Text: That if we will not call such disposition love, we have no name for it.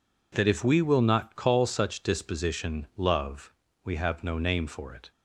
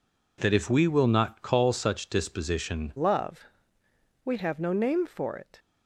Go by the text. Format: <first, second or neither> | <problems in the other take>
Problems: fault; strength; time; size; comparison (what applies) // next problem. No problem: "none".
first | changes voice at "love"; from 2.9 s on; 2.6 s long